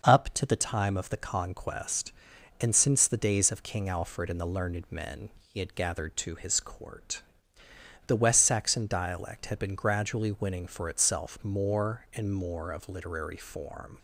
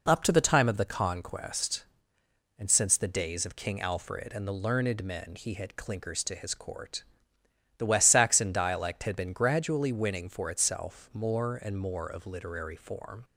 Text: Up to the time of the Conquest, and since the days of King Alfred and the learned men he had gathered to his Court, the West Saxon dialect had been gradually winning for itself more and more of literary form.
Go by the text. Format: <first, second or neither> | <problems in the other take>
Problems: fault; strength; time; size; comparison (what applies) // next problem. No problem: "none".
first | says "clinkers" for "gathered"; at 5.7 s